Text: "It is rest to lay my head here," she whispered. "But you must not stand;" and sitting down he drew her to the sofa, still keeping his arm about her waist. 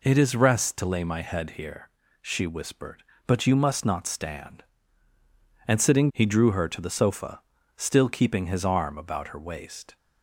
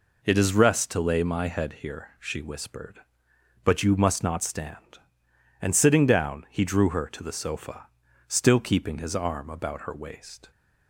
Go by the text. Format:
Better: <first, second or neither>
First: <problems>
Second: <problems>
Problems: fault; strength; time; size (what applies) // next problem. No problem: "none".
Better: second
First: skips "down"; at 6.1 s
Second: none